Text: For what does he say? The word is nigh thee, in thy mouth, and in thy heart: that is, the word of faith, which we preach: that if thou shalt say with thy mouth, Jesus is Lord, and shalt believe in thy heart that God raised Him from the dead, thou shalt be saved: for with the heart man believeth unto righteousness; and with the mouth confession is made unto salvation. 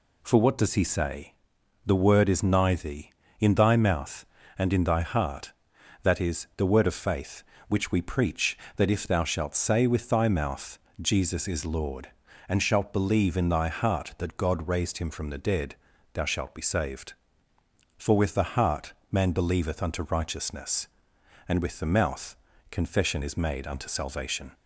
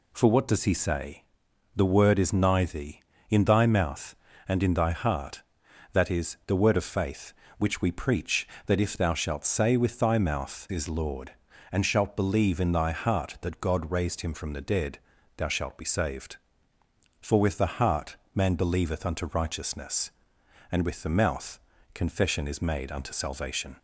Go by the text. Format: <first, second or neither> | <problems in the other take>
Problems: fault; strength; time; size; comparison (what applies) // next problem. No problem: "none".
first | skips "Jesus"; at 10.6 s // pauses between "heart" and "man"; slight; at 18.1 s; 0.18 s long; slight in the first // pauses between "mouth" and "confession"; slight; at 21.5 s; 0.32 s long; slight in the first